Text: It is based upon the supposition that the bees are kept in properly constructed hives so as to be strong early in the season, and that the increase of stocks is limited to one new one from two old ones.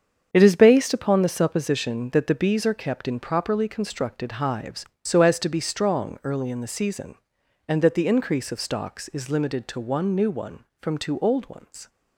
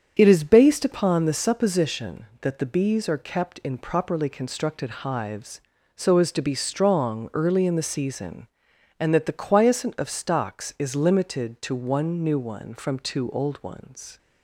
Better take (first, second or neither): first